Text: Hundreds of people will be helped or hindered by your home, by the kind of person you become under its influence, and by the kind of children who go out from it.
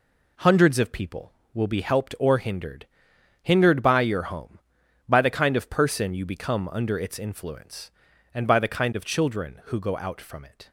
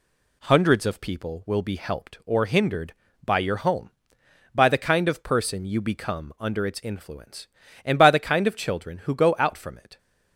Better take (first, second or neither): second